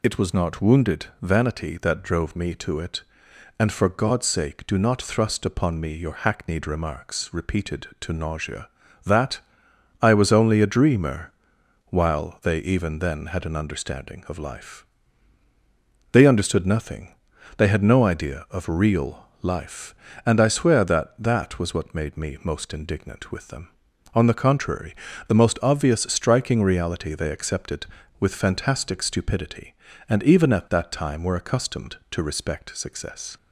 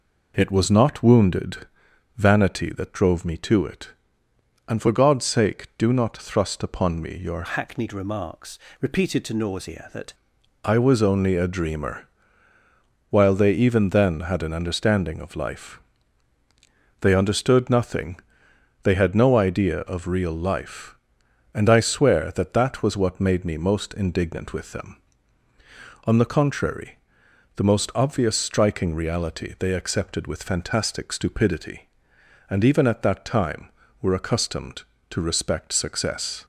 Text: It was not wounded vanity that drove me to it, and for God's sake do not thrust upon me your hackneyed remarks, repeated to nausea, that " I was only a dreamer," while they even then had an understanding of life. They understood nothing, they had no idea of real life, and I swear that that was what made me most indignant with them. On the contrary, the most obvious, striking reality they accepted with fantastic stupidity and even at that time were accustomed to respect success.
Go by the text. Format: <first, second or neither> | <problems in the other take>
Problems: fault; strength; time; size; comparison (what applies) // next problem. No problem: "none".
first | pauses between "wounded" and "vanity"; noticeable; at 1.6 s; 0.52 s long; slight in the first // changes voice from "hackneyed" to "that"; from 7.4 to 10.1 s; 2.7 s long